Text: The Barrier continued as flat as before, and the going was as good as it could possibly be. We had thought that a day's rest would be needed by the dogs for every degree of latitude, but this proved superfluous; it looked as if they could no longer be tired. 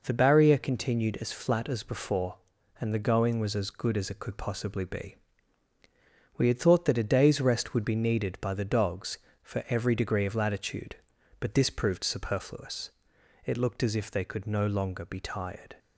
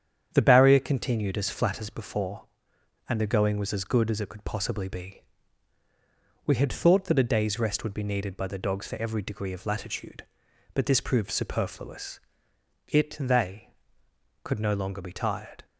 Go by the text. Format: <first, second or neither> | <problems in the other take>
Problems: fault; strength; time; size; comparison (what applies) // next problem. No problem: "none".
first | starts louder than the rest; strong; until 1.3 s; 8.5 dB // skips "looked as if"; at 13.1 s